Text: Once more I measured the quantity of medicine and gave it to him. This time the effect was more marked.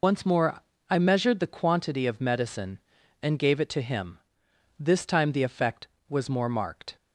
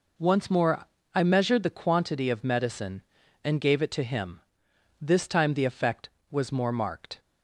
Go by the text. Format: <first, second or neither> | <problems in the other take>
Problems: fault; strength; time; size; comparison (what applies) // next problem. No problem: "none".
second | loses the start of "Once"; at 0.0 s; 100 ms // pauses between "more" and "I"; slight; at 0.6 s; 0.28 s long; slight in the second